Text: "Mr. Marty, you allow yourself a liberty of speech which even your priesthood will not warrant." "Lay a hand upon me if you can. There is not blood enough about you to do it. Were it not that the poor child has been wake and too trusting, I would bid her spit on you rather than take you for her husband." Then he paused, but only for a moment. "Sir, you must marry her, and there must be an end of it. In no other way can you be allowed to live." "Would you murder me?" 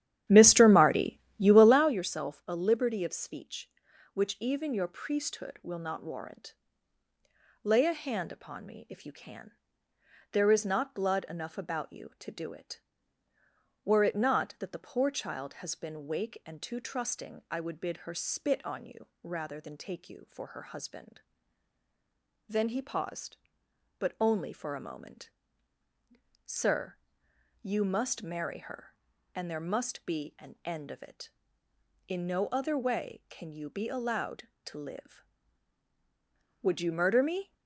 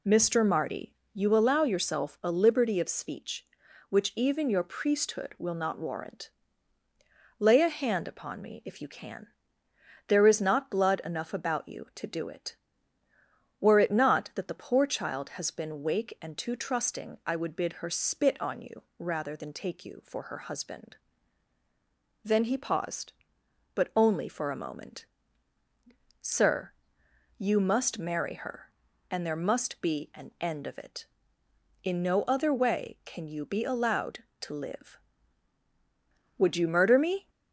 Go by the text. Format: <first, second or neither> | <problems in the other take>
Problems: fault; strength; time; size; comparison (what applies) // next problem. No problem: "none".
second | starts louder than the rest; strong; until 2.0 s; 11.5 dB // pauses between "you" and "rather"; slight; at 19.0 s; 0.16 s long; slight in the second